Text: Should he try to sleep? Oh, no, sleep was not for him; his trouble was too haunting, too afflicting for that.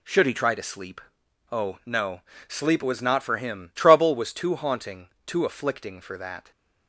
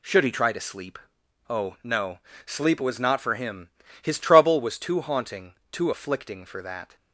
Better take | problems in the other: second | skips "his"; at 3.7 s

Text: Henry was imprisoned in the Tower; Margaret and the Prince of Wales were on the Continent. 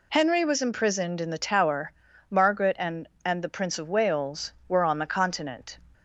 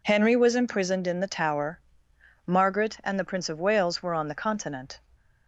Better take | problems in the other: second | says "and" twice; at 3.2 s

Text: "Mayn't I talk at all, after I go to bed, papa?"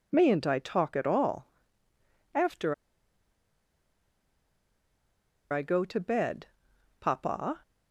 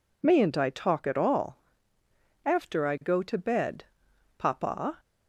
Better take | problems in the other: second | pauses between "after" and "I"; strong; at 2.7 s; 2.7 s long

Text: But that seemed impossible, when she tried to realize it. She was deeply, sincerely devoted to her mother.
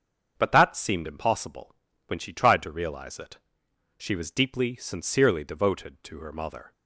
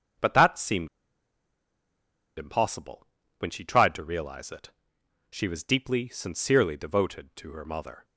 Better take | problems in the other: first | starts louder than the rest; strong; until 2.7 s; 7 dB; strong in the first // pauses between "seemed" and "impossible"; strong; at 0.8 s; 1.5 s long

